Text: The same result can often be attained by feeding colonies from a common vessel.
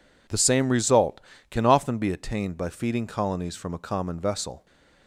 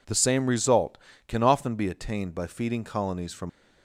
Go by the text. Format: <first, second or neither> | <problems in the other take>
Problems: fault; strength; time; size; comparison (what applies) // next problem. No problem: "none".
first | stops before "a common vessel"; at 3.4 s